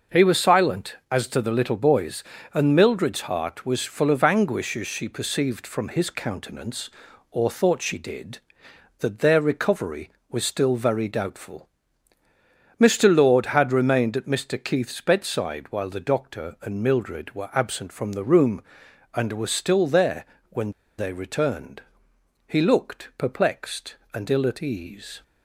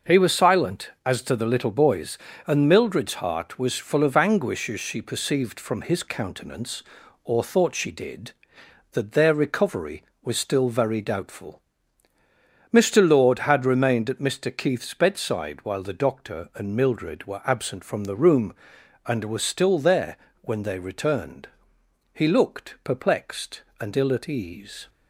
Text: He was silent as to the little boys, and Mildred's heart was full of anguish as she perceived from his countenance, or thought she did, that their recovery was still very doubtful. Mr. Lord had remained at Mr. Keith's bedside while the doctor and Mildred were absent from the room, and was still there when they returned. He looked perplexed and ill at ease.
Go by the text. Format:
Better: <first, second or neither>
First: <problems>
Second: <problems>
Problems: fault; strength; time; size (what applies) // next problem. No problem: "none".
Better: second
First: pauses between "there" and "when"; slight; at 20.2 s; 0.26 s long // pauses between "when" and "they"; slight; at 20.7 s; 0.27 s long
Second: pauses between "there" and "when"; slight; at 20.1 s; 0.26 s long